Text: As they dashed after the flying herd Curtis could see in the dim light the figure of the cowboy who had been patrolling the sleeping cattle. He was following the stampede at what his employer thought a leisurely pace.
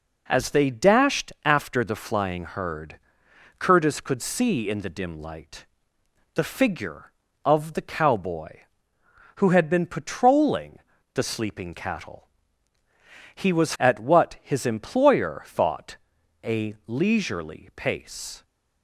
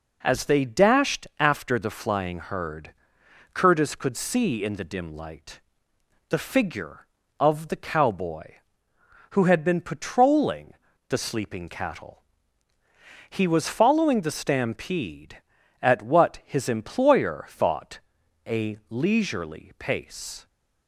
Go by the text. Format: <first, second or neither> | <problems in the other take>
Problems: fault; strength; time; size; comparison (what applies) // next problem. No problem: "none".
second | pauses between "herd" and "Curtis"; noticeable; at 2.9 s; 0.62 s long; noticeable in the second // pauses between "light" and "the"; noticeable; at 5.6 s; 0.68 s long; noticeable in the second // pauses between "patrolling" and "the"; slight; at 10.7 s; 0.36 s long; slight in the second // skips "following the stampede"; at 13.7 s // pauses between "thought" and "a"; noticeable; at 15.9 s; 0.48 s long; noticeable in the second